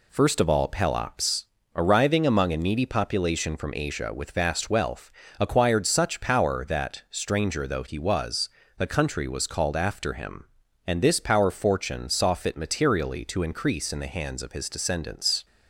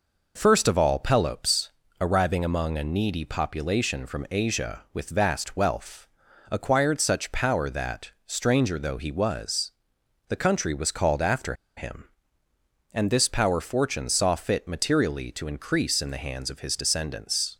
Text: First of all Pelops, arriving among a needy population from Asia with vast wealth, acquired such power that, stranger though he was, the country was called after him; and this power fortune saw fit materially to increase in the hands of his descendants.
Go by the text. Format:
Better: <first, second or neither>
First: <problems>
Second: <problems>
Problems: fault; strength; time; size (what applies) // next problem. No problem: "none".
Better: first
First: none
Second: pauses between "after" and "him"; slight; at 11.5 s; 0.22 s long